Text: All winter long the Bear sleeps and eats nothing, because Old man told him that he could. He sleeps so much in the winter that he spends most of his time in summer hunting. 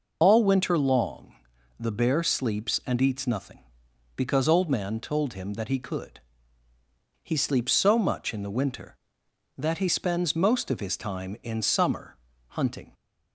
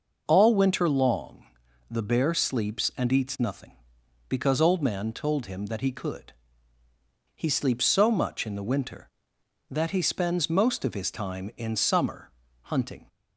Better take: second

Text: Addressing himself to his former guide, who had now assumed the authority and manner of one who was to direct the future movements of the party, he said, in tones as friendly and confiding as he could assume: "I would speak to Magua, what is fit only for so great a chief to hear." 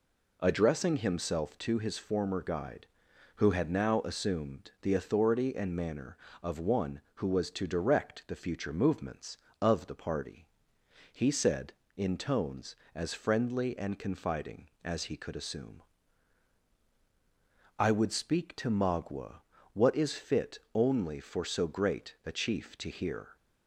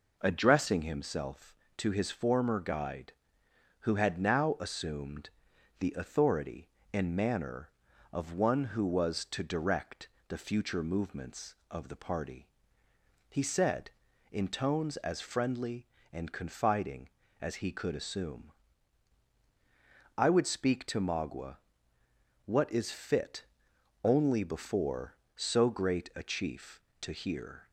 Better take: first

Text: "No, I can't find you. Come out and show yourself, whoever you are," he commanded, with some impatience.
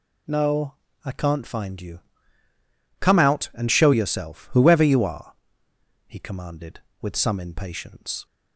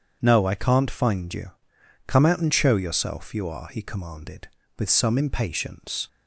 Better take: first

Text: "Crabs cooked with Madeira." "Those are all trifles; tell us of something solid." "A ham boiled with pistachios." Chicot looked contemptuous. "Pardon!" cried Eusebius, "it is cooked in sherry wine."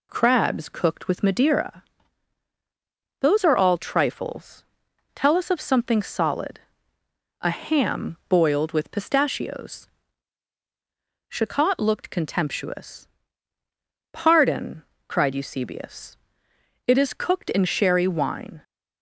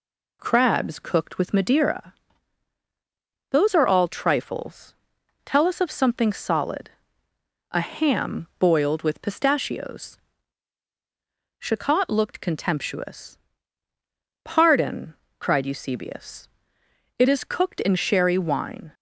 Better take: neither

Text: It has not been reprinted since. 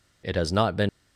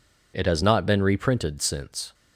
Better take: second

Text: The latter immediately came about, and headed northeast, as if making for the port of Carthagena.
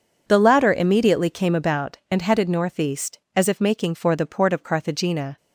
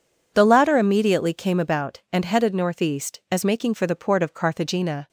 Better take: first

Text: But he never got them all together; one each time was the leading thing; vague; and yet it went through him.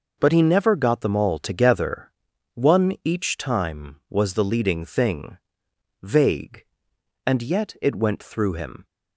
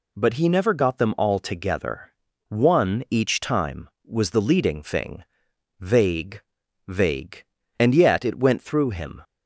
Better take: first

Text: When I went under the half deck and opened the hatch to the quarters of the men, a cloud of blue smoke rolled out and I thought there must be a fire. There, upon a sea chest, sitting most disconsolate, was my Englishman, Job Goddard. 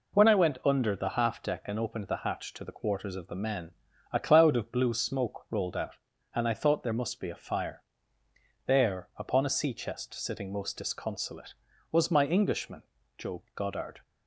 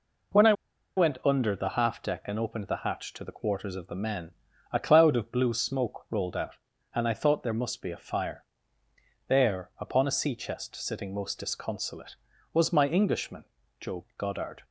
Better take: first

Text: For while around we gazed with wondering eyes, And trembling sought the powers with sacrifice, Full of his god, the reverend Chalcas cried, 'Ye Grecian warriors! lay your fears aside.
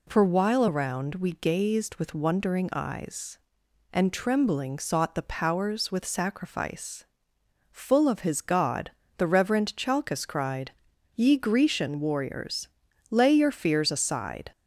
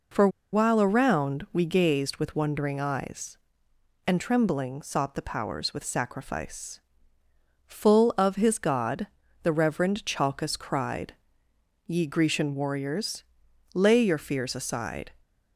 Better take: first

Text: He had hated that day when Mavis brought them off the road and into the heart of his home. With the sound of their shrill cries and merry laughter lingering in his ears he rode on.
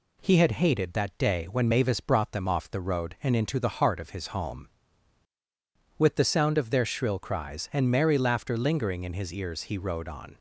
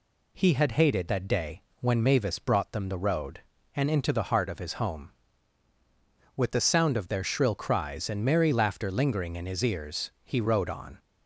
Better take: first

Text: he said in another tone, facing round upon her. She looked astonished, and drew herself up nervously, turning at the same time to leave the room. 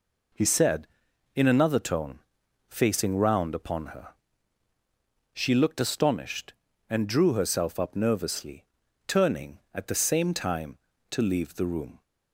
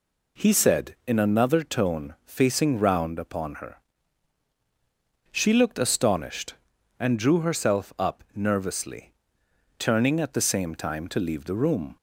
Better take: neither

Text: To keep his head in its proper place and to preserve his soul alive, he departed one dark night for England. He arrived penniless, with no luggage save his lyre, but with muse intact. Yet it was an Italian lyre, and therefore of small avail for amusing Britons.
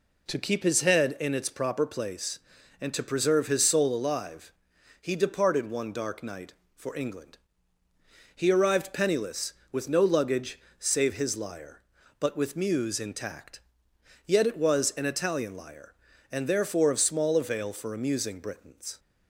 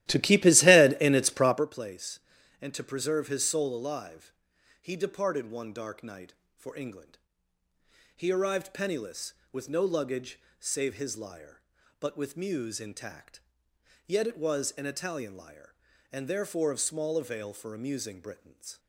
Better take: first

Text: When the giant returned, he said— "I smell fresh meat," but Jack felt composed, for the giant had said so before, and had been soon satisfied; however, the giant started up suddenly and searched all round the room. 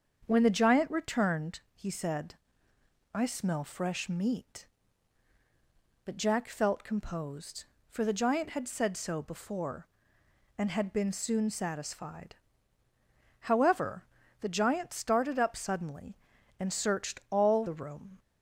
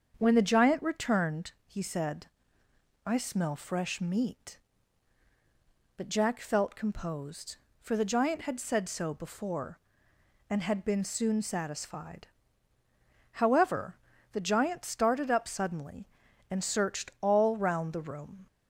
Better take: second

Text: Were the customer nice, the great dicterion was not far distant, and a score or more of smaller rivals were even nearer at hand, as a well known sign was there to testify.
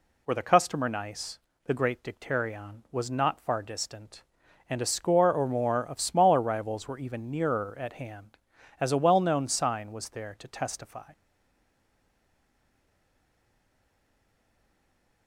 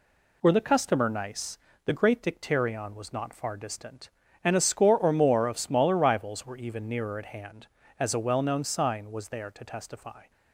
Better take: second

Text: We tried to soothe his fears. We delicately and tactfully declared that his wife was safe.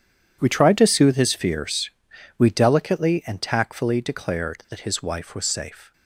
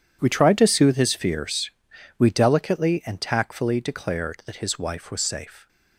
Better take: neither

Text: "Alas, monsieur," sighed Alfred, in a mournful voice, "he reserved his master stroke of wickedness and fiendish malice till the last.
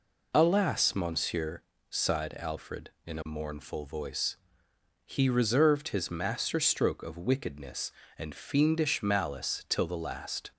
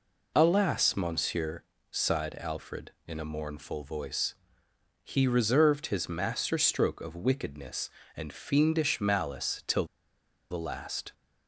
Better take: first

